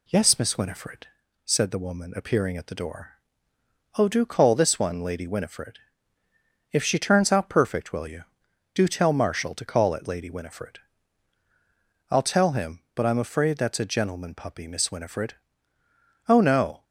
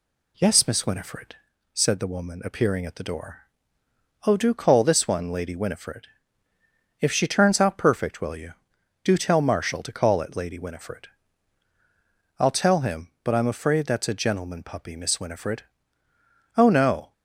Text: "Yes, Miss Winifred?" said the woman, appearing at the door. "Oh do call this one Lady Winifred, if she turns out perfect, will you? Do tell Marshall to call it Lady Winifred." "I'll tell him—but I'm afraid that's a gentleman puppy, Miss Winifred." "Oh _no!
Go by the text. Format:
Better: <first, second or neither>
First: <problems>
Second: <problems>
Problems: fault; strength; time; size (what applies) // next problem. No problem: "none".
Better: neither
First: none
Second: none